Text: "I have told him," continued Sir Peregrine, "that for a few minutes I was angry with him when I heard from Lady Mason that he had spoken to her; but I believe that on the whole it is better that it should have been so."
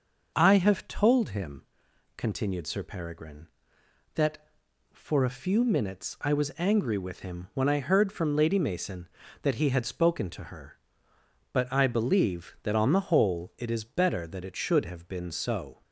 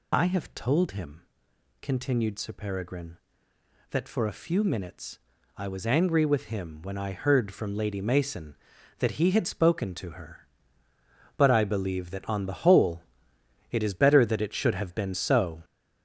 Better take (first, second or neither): first